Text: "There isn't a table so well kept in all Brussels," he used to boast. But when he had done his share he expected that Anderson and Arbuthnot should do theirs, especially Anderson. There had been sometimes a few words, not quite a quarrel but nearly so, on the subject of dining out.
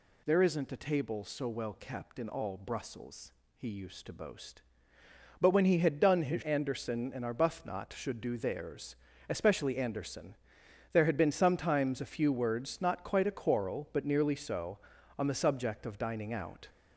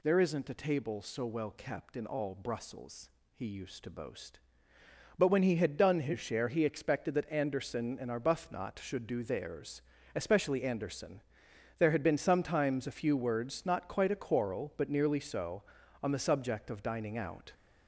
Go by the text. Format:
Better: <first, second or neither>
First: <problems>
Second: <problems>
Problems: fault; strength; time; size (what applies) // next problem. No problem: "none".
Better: second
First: skips "share he expected that"; at 6.4 s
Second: none